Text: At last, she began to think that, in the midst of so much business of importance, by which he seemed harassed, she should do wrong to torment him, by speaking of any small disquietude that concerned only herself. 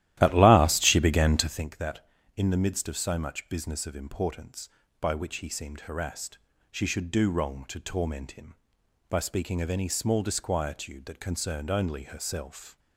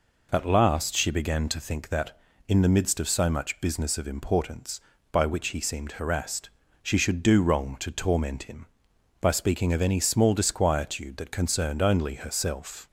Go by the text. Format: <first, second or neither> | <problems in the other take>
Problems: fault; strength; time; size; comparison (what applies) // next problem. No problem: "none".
second | starts louder than the rest; strong; until 1.7 s; 14 dB